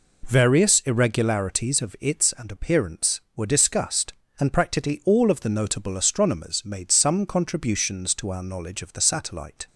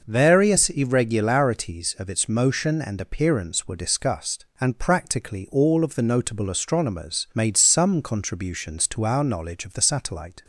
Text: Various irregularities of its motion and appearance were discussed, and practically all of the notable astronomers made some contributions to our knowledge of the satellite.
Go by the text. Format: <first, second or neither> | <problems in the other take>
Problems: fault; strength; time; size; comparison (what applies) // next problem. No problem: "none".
second | skips "motion"; at 2.3 s